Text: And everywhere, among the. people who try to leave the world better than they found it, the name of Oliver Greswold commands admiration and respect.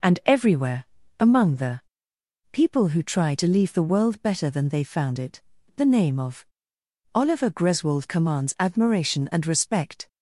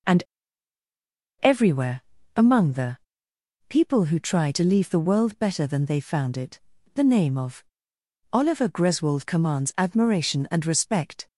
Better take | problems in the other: first | pauses between "And" and "everywhere"; at 0.2 s; 1.1 s long // pauses between "of" and "Oliver"; noticeable; at 7.6 s; 0.68 s long; noticeable in the first

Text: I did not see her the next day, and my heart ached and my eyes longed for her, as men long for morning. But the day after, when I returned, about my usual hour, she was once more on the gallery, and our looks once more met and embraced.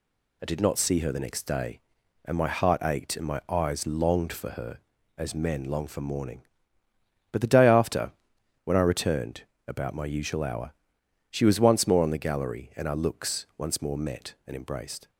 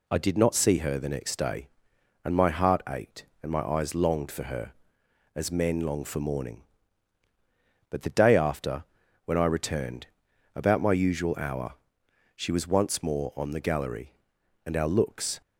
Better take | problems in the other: first | stops before "once more met and embraced"; at 15.4 s

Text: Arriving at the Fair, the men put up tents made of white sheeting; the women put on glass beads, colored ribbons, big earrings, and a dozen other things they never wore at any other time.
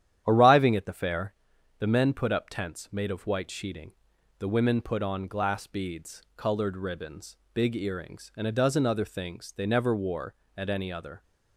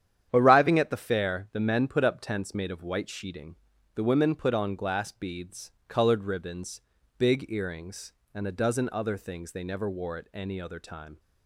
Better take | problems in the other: second | starts louder than the rest; strong; until 1.2 s; 10.5 dB; strong in the second // stops before "time"; at 11.2 s

